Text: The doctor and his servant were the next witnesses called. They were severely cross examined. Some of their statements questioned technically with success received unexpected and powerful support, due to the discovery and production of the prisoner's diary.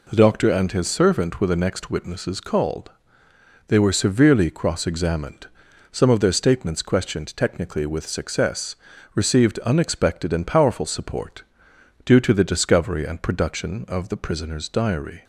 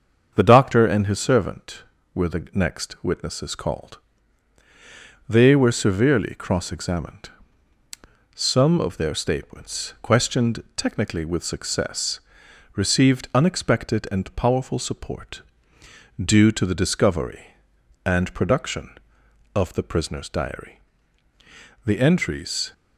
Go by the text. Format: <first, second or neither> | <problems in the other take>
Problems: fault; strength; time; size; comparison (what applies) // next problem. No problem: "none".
first | starts louder than the rest; until 1.3 s; 7 dB // pauses between "success" and "received"; noticeable; at 12.1 s; 0.56 s long; also in the first // goes on to say "The entries"; noticeable; from 21.8 s on; 0.88 s long